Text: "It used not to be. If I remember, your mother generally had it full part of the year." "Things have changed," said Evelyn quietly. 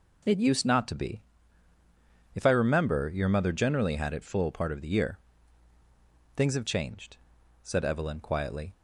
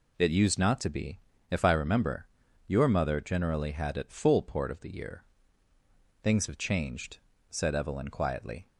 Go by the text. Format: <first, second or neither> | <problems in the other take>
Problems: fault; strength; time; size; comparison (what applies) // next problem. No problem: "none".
first | says "port" for "part"; at 4.4 s